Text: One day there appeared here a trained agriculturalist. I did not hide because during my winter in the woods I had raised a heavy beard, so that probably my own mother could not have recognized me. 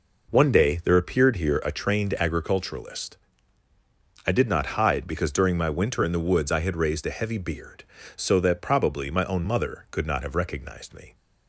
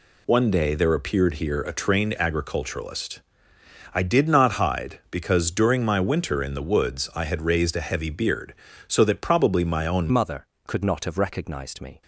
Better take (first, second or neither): first